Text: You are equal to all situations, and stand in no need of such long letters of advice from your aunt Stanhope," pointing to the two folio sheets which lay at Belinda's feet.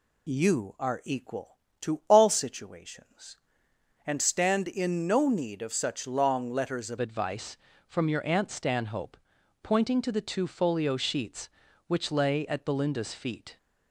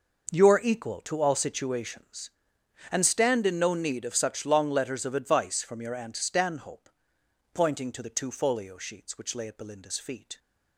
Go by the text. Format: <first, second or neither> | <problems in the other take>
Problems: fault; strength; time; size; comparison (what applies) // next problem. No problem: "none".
second | changes voice at "advice"; from 6.9 s on; 6.6 s long